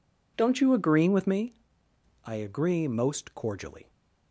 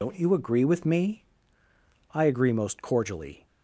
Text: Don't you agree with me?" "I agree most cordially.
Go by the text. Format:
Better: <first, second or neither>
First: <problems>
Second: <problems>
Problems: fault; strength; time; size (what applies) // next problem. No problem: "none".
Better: first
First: none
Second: loses the start of "Don't"; at 0.0 s; 45 ms